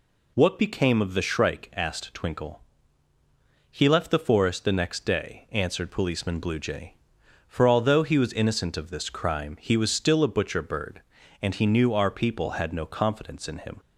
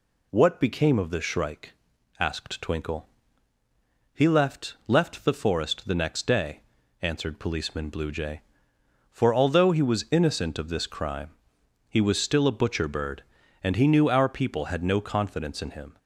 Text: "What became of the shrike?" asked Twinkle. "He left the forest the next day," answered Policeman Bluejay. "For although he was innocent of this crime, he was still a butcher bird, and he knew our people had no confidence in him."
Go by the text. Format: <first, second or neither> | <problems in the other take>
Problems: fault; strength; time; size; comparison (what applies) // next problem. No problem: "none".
first | says "left" twice; at 4.8 s